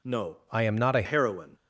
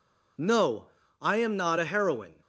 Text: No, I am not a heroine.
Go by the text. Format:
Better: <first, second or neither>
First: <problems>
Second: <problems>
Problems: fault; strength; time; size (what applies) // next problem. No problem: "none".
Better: second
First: changes voice from "I" to "a"; from 0.4 to 1.0 s; 0.6 s long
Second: none